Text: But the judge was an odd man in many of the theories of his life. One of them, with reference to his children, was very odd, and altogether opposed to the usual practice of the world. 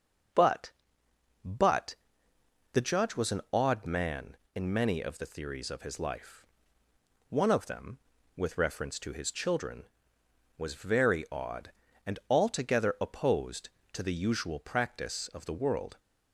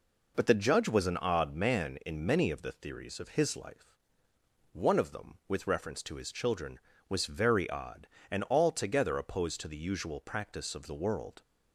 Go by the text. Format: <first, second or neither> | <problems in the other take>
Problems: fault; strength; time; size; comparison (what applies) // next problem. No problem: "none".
second | says "But" twice; at 1.4 s